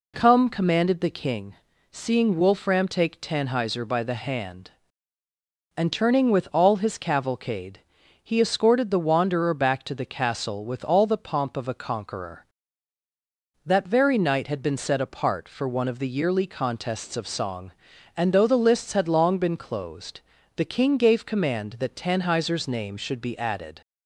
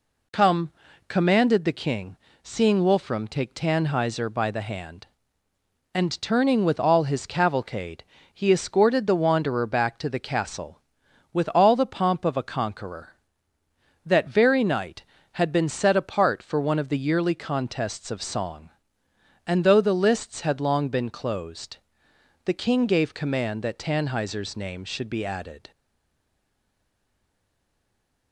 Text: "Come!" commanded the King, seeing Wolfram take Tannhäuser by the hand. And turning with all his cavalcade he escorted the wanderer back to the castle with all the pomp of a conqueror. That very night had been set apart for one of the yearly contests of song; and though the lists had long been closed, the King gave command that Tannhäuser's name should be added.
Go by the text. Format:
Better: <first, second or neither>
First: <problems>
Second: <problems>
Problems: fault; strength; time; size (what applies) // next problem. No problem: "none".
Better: first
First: pauses between "cavalcade" and "he"; at 7.8 s; 0.42 s long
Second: pauses between "cavalcade" and "he"; slight; at 8.0 s; 0.32 s long // stays silent after the last word; strong; from 25.7 s on; 2.6 s long